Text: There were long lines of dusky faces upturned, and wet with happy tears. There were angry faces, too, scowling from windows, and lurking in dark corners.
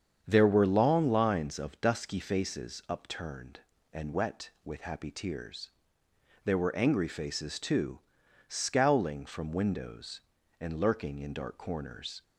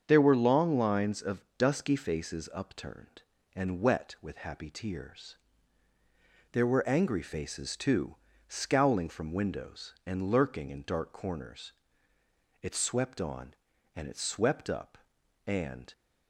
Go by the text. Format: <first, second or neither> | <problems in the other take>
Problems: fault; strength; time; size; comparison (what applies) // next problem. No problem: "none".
first | starts louder than the rest; strong; until 1.0 s; 7 dB; strong in the first // goes on to say "It swept on and it swept up and"; strong; from 12.6 s on; 3.3 s long